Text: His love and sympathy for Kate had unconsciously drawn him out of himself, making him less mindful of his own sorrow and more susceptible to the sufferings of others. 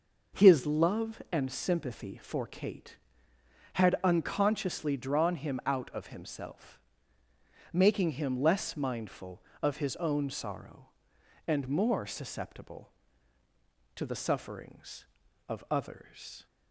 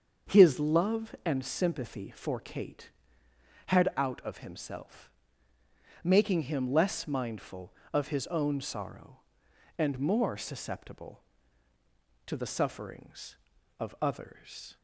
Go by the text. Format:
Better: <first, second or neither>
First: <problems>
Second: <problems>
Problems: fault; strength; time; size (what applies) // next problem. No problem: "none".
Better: first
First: none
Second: starts louder than the rest; until 1.3 s; 7 dB // skips "unconsciously drawn him"; at 3.9 s